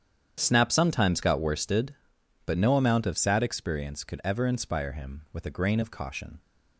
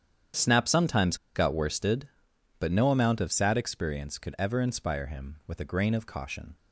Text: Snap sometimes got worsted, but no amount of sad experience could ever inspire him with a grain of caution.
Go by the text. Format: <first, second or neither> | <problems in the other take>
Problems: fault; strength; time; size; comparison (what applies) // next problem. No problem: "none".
first | starts louder than the rest; strong; until 1.5 s; 9 dB; strong in the first // pauses between "sometimes" and "got"; slight; at 1.1 s; 0.20 s long